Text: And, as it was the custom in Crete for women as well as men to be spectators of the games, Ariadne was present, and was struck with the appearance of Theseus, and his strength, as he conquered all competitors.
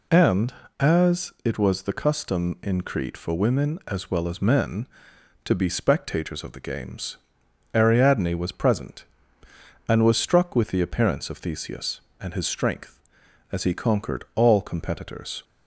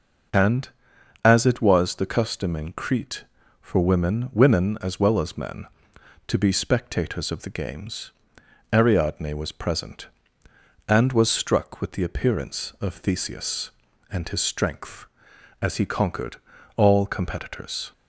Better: first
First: none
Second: says "women" twice; at 4.3 s // pauses between "conquered" and "all"; at 16.3 s; 0.40 s long

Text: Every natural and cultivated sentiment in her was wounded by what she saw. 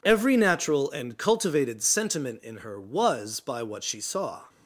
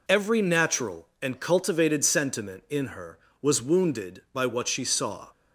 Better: second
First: skips "wounded"; at 3.3 s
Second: none

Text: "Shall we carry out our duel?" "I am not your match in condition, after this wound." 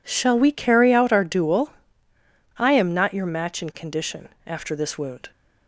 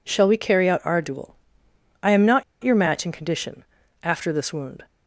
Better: first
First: none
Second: pauses between "not" and "your"; slight; at 2.4 s; 0.18 s long

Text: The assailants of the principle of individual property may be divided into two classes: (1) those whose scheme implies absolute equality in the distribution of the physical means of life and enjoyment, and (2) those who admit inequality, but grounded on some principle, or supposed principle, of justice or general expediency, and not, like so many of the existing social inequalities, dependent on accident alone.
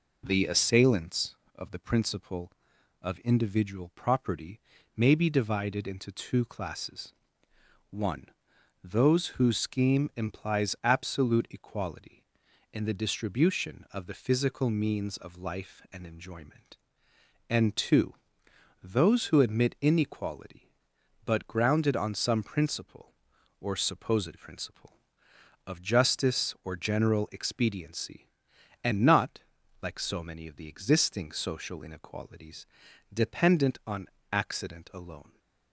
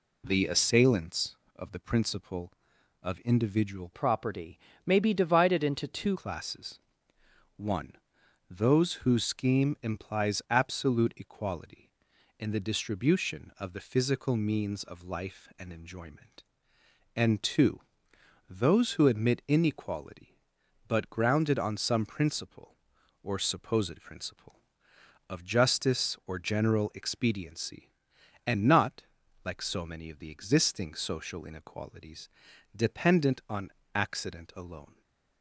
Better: first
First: pauses between "property" and "may"; at 4.5 s; 0.38 s long // pauses between "on" and "accident"; slight; at 34.0 s; 0.24 s long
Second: changes voice from "property" to "two"; from 3.9 to 6.1 s; 2.2 s long // pauses between "property" and "may"; slight; at 4.5 s; 0.28 s long // pauses between "on" and "accident"; slight; at 33.7 s; 0.24 s long

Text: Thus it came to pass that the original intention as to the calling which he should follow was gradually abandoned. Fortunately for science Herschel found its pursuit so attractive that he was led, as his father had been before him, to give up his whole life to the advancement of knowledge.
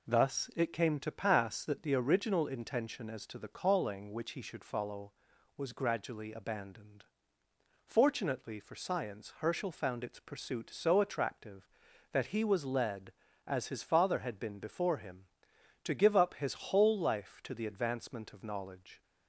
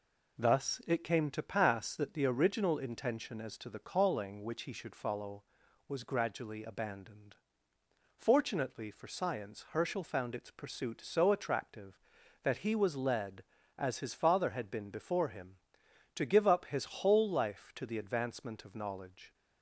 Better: neither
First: none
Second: none

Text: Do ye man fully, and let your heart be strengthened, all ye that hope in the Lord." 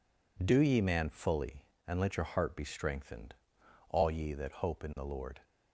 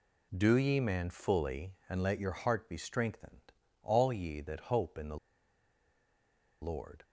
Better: first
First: none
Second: pauses between "the" and "Lord"; strong; at 5.1 s; 1.4 s long

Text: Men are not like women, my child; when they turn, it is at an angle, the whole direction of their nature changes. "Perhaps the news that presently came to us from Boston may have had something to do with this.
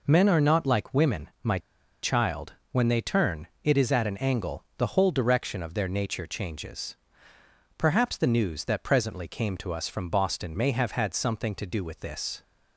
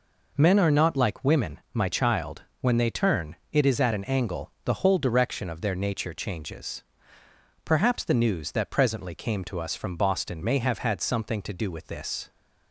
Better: second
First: pauses between "my" and "child"; at 1.5 s; 0.44 s long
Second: none

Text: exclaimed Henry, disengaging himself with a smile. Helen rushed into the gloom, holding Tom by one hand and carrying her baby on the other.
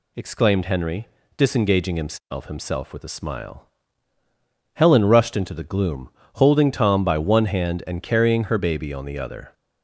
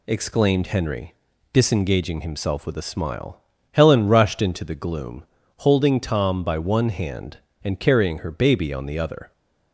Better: second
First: says "himself" twice; at 2.4 s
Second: none

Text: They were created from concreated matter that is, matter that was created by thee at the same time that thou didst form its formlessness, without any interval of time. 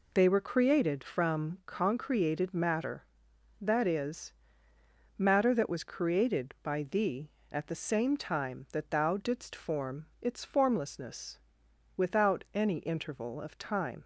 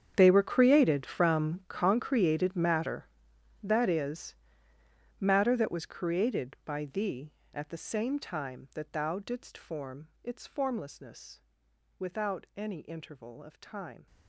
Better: first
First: pauses between "form" and "its"; slight; at 10.0 s; 0.16 s long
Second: gets quieter; strong; throughout; 19.5 dB // pauses between "form" and "its"; slight; at 10.0 s; 0.16 s long

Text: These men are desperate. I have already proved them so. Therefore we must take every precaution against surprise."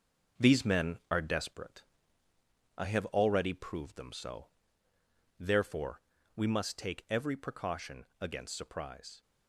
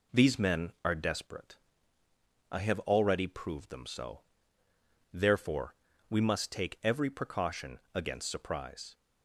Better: second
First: gets quieter; throughout; 6 dB // pauses between "Therefore" and "we"; slight; at 6.0 s; 0.34 s long // pauses between "precaution" and "against"; slight; at 8.0 s; 0.16 s long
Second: pauses between "Therefore" and "we"; slight; at 5.7 s; 0.34 s long // pauses between "precaution" and "against"; slight; at 7.7 s; 0.16 s long

